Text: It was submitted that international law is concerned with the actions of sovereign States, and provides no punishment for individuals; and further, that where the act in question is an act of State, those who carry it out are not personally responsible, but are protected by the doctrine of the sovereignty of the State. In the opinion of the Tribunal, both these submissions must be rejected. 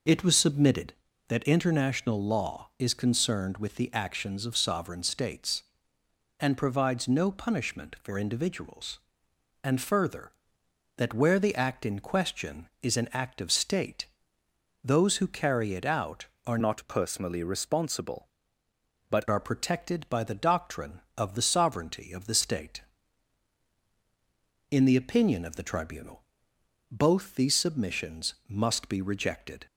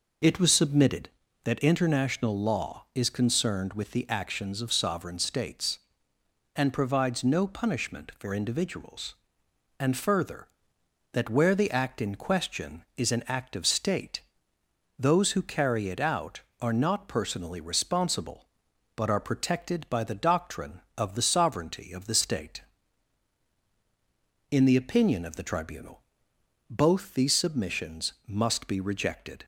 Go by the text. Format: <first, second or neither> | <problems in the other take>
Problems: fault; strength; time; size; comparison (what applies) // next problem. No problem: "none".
second | changes voice from "not" to "but"; from 16.6 to 19.2 s; 2.6 s long